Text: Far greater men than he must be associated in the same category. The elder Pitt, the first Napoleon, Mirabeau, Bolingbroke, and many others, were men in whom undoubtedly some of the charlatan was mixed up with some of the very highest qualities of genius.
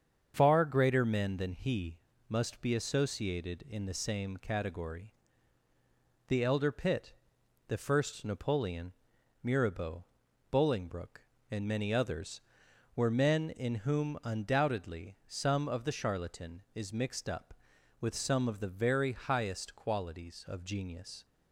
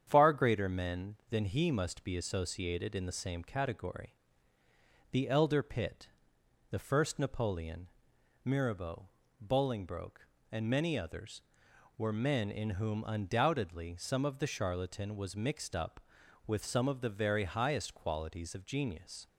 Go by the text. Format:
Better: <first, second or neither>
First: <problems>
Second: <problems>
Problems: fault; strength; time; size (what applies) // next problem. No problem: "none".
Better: second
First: starts louder than the rest; strong; until 1.3 s; 7.5 dB // pauses between "he" and "must"; slight; at 1.9 s; 0.29 s long // says "is" for "was"; at 16.7 s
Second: starts louder than the rest; strong; until 1.0 s; 8.5 dB